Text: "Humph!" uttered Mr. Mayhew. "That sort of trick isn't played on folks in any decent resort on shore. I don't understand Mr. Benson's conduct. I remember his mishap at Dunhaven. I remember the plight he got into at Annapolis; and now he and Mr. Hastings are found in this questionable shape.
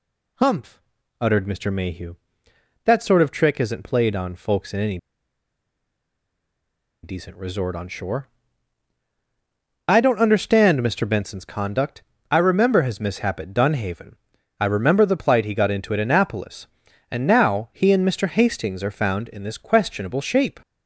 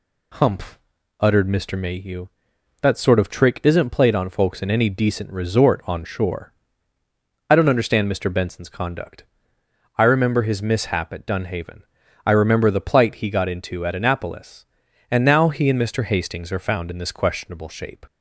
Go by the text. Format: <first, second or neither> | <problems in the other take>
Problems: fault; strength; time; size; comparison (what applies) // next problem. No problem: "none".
second | pauses between "any" and "decent"; strong; at 4.9 s; 2.0 s long